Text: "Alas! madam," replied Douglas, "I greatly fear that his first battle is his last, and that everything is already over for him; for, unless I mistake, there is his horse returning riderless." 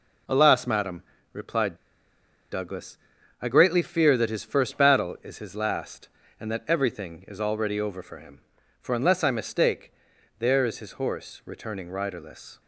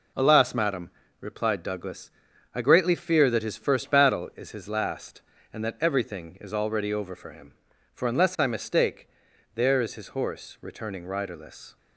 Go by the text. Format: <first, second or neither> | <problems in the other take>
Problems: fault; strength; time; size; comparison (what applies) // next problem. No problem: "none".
second | pauses between "replied" and "Douglas"; noticeable; at 1.7 s; 0.76 s long